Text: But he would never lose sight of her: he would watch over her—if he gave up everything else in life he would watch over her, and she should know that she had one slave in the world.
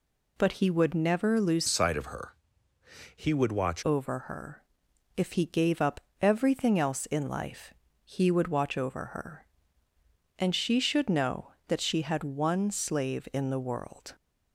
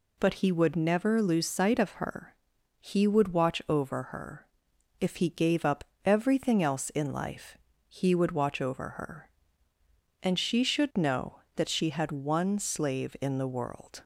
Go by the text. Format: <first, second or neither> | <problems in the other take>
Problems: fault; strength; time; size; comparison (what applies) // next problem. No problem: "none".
second | changes voice from "sight" to "watch"; from 1.6 to 3.8 s; 2.2 s long // pauses between "up" and "everything"; slight; at 5.9 s; 0.20 s long; slight in the second // pauses between "life" and "he"; slight; at 7.7 s; 0.32 s long; slight in the second